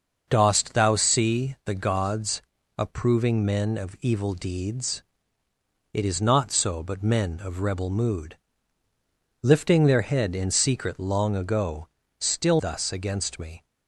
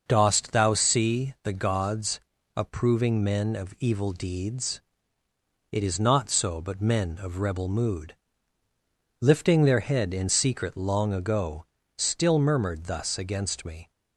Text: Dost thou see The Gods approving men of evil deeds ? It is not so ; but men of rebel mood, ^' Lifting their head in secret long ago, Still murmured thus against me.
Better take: second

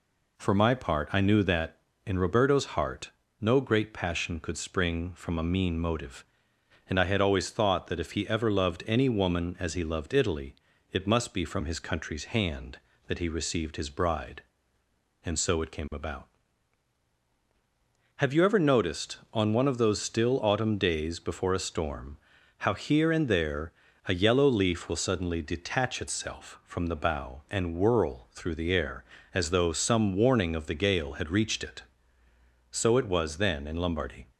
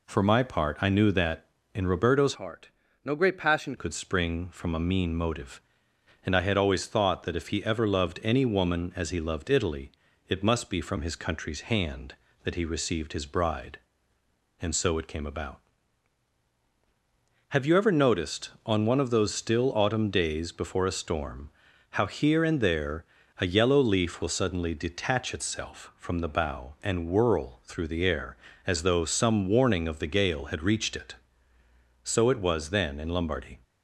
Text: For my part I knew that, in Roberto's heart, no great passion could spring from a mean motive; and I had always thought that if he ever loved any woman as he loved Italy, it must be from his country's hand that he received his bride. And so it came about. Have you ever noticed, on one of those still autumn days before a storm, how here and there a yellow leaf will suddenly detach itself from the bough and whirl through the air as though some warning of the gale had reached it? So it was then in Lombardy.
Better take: first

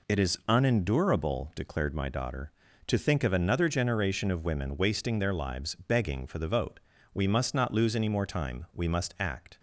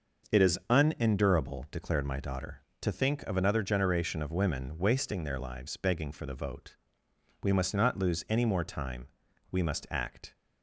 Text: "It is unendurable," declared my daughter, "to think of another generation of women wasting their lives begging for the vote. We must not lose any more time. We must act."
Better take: neither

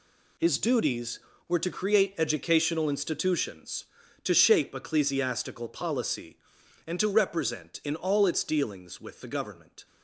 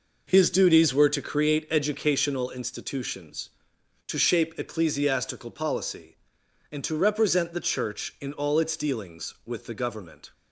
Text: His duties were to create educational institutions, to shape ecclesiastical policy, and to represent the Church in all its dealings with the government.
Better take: second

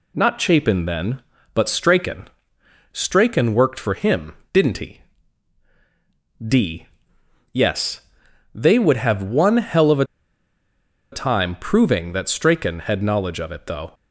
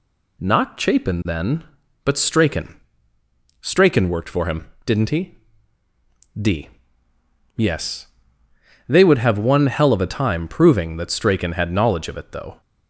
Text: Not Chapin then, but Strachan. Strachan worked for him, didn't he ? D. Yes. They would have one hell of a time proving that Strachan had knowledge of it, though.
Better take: second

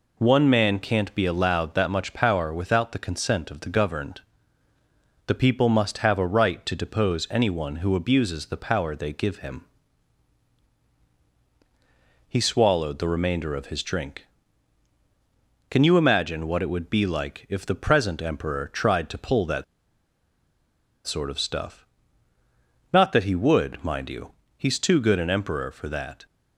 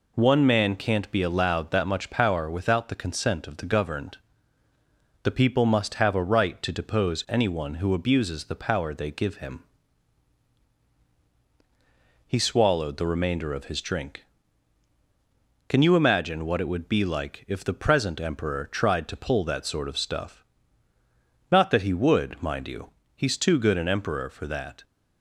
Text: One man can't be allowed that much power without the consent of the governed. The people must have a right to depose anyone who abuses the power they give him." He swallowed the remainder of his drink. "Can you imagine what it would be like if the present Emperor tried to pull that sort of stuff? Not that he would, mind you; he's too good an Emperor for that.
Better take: second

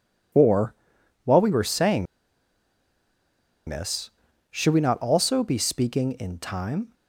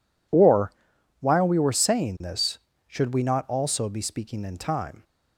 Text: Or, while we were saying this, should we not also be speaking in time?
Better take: second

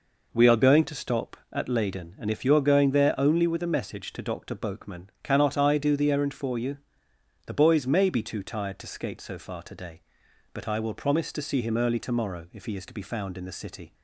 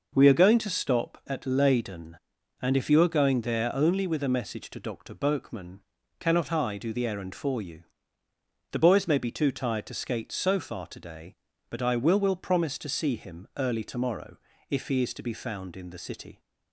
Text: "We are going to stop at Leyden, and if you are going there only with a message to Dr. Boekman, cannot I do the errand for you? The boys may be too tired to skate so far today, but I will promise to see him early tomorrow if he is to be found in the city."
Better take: first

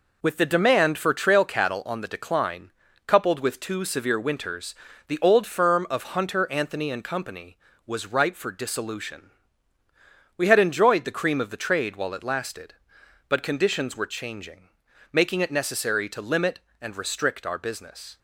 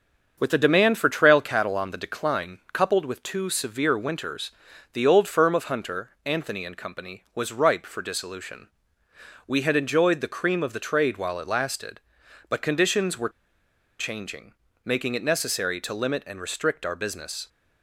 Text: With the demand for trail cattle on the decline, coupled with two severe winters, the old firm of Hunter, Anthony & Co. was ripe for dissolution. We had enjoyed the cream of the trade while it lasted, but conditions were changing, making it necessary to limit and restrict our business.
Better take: first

